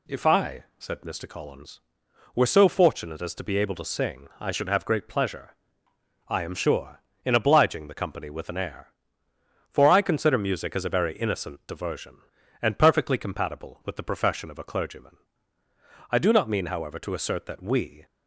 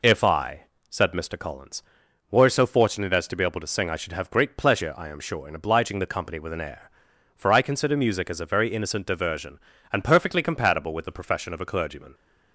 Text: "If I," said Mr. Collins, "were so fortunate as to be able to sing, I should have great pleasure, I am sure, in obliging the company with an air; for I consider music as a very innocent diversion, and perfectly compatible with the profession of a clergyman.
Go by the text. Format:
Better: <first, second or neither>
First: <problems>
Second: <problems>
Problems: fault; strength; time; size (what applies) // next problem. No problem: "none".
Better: second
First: goes on to say "I do not mean however to assert that we"; strong; from 16.0 s on; 1.9 s long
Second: none